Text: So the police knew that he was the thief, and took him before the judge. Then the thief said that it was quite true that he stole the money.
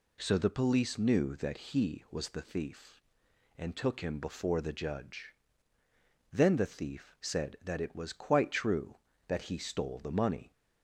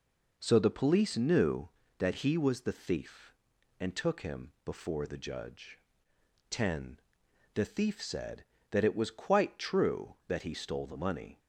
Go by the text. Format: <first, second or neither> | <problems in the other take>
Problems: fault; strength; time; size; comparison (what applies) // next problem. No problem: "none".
first | says "Ten" for "Then"; at 6.5 s